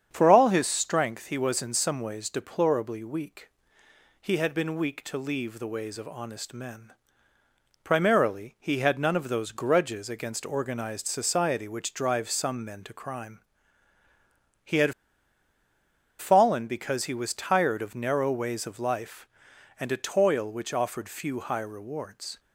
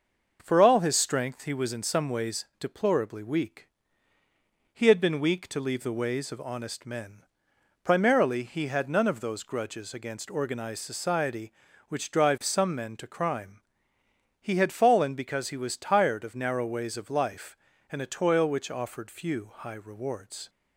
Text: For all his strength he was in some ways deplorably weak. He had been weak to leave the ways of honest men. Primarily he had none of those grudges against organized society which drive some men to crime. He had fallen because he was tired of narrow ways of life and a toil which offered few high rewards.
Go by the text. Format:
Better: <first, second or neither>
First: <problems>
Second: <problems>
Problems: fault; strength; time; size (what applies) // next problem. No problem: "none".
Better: second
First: starts louder than the rest; strong; until 1.1 s; 8 dB // pauses between "had" and "fallen"; strong; at 14.9 s; 1.2 s long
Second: starts louder than the rest; until 1.4 s; 6 dB